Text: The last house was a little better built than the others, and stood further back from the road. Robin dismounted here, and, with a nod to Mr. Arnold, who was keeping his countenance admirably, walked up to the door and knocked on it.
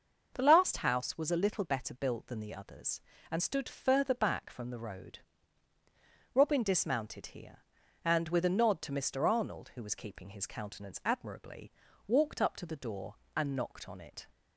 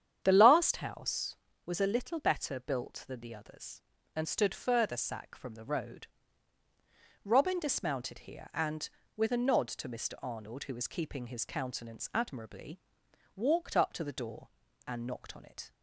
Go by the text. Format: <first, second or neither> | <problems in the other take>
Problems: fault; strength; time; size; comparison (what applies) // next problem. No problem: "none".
first | starts louder than the rest; strong; until 1.2 s; 9 dB; noticeable in the first // says "sack" for "back"; at 4.9 s